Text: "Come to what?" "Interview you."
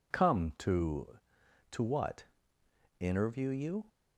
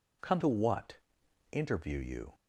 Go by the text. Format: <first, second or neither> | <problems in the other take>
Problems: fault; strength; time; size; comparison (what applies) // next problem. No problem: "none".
second | says "to" twice; at 1.7 s